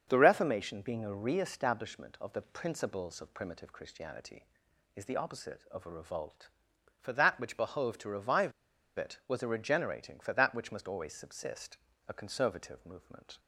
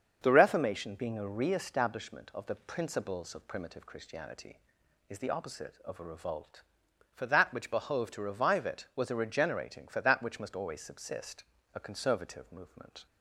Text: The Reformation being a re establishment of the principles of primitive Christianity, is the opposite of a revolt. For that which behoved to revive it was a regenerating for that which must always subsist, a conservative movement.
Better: second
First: starts louder than the rest; until 1.0 s; 7 dB // pauses between "revive" and "it"; noticeable; at 8.5 s; 0.47 s long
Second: starts louder than the rest; until 1.2 s; 6.5 dB

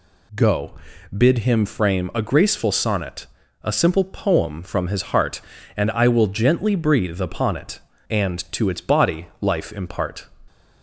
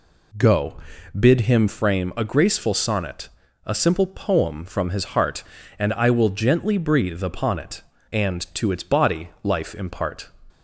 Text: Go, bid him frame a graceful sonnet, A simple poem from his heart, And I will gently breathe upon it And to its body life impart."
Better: first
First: none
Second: starts louder than the rest; slight; until 1.9 s; 2.5 dB

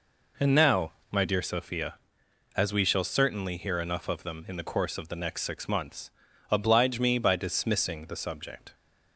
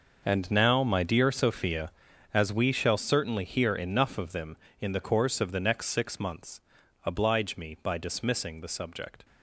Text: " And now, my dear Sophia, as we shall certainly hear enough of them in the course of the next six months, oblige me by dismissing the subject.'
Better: first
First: none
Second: gets quieter; strong; throughout; 13 dB

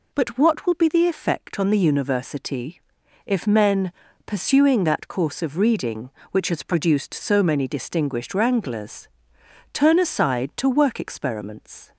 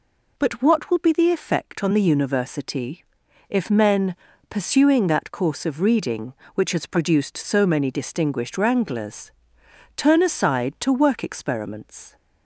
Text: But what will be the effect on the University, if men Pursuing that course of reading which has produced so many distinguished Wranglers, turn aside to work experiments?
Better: neither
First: pauses between "men" and "Pursuing"; slight; at 3.9 s; 0.32 s long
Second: pauses between "men" and "Pursuing"; slight; at 4.1 s; 0.32 s long

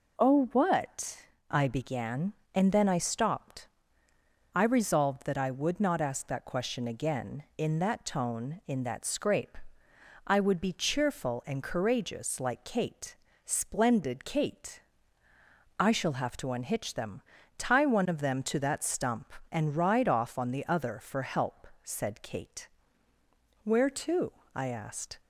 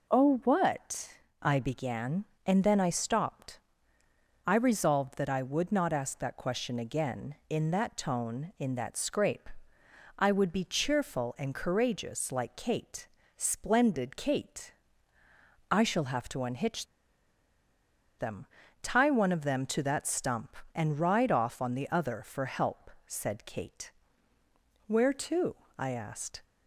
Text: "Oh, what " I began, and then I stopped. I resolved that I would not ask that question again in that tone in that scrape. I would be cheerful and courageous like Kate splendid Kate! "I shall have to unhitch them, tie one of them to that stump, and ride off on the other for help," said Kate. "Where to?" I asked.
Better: first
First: pauses between "Kate" and "splendid"; slight; at 13.1 s; 0.30 s long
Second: pauses between "Kate" and "splendid"; slight; at 13.0 s; 0.30 s long // pauses between "unhitch" and "them"; strong; at 16.8 s; 1.3 s long

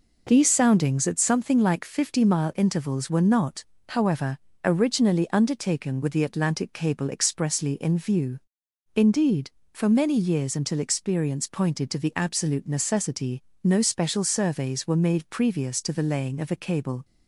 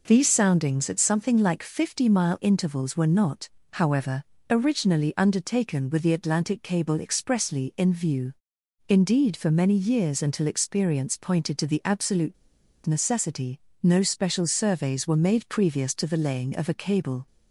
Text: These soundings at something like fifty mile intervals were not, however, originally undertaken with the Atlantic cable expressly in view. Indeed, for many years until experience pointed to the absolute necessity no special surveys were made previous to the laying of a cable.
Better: first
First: pauses between "necessity" and "no"; slight; at 13.4 s; 0.21 s long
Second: pauses between "absolute" and "necessity"; noticeable; at 12.3 s; 0.51 s long // pauses between "necessity" and "no"; slight; at 13.5 s; 0.24 s long

